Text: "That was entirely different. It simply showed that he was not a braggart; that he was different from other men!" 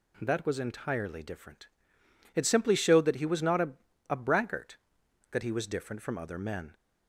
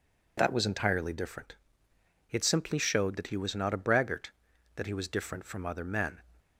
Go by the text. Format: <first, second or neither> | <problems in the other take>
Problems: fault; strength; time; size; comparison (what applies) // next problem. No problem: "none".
second | says "a" twice; at 4.0 s